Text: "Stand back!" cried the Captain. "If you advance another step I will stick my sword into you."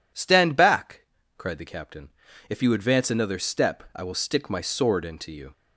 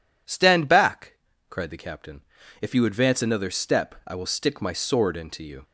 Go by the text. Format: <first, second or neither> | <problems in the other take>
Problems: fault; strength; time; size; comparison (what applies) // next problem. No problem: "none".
neither | none